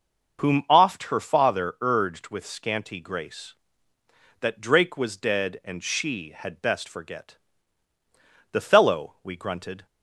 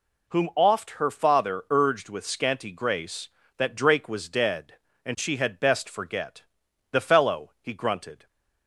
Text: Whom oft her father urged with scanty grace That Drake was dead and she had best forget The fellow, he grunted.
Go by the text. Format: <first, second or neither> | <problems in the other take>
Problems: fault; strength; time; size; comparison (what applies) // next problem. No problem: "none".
second | starts louder than the rest; until 1.4 s; 6 dB // pauses between "forget" and "The"; at 7.3 s; 1.1 s long; noticeable in the second // says "we" for "he"; at 9.2 s